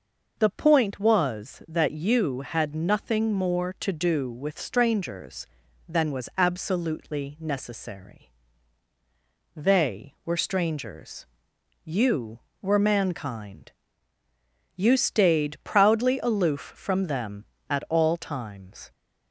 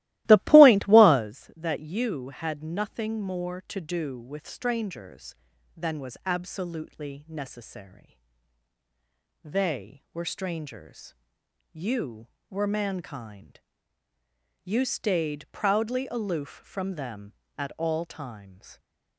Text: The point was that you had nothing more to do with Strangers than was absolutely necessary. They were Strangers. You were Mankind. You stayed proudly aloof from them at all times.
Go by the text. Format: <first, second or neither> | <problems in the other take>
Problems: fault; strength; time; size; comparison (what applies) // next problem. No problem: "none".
first | starts louder than the rest; strong; until 1.3 s; 17 dB